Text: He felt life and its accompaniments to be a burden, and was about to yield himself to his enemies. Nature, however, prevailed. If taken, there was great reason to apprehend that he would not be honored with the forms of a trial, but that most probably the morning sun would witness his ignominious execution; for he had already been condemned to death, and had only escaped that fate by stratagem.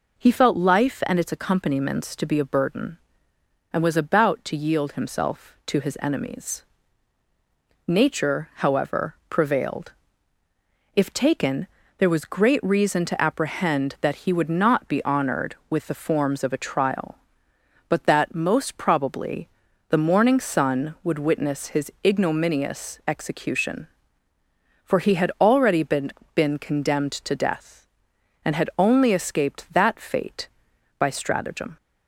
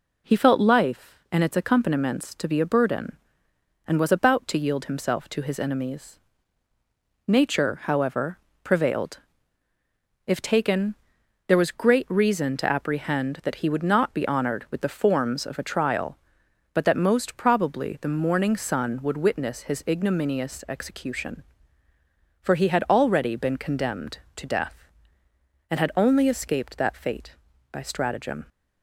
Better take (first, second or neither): second